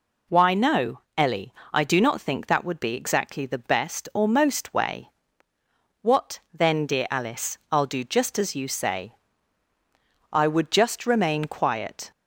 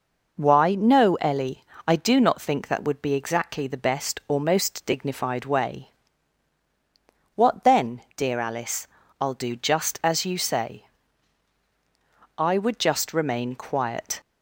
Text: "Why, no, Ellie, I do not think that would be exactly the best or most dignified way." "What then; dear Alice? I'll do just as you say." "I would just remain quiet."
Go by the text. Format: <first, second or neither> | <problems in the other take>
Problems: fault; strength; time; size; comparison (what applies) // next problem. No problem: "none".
second | skips "dignified"; at 4.7 s